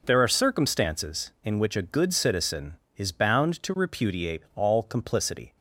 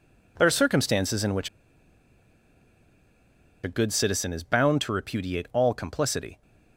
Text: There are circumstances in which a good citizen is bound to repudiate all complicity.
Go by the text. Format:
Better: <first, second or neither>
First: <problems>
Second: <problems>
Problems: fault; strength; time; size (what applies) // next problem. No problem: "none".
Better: first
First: none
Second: pauses between "which" and "a"; strong; at 1.4 s; 2.1 s long